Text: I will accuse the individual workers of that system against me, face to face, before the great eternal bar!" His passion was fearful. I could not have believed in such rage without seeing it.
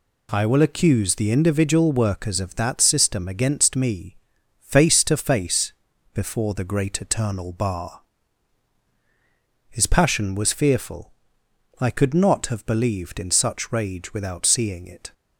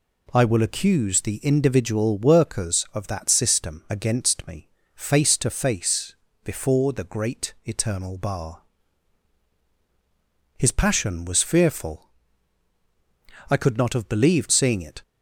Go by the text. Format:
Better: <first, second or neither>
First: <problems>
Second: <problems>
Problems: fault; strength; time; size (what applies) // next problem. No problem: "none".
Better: first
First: none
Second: skips "in such rage without"; at 14.5 s